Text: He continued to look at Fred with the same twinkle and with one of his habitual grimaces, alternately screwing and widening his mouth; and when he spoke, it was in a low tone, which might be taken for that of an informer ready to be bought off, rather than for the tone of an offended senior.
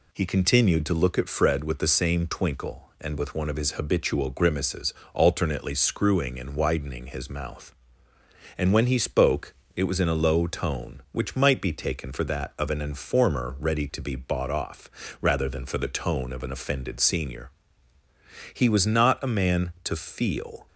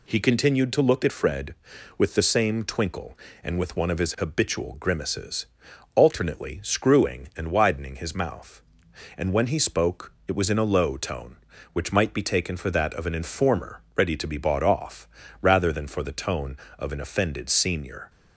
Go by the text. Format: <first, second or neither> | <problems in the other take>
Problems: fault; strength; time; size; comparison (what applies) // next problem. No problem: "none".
second | goes on to say "He was not a man to feel"; strong; from 18.5 s on; 2.1 s long